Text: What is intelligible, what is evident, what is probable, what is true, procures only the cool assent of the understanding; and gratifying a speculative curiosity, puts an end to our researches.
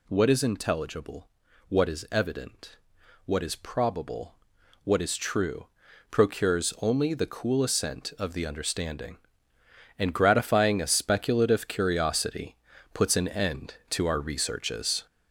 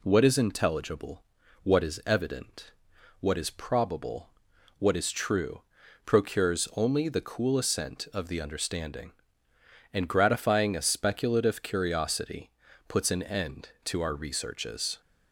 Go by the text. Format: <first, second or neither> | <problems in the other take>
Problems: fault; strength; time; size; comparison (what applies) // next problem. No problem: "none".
second | gets louder; noticeable; throughout; 6 dB